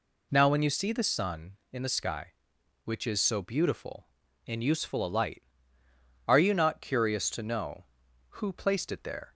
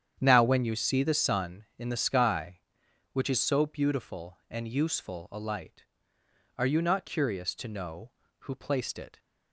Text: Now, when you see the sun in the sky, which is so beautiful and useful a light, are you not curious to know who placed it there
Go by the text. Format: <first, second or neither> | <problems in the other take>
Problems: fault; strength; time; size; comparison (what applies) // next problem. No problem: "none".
first | starts louder than the rest; strong; until 1.2 s; 9 dB // stops before "there"; at 9.1 s